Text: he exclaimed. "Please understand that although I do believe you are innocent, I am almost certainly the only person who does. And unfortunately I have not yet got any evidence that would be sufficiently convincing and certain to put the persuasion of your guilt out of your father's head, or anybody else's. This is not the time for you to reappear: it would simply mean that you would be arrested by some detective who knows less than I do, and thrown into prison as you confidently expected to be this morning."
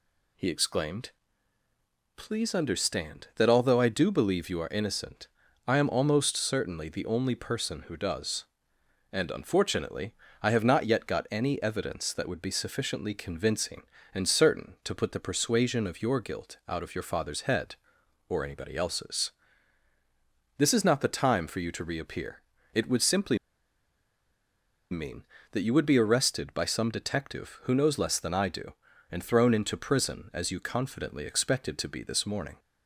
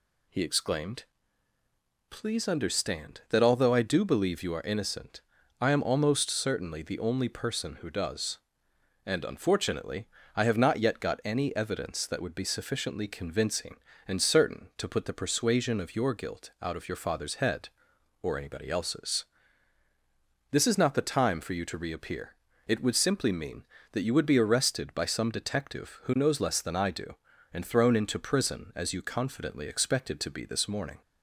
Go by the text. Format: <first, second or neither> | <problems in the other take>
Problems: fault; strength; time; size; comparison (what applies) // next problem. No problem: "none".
second | pauses between "unfortunately" and "I"; slight; at 10.1 s; 0.28 s long; slight in the second // pauses between "simply" and "mean"; strong; at 23.3 s; 1.5 s long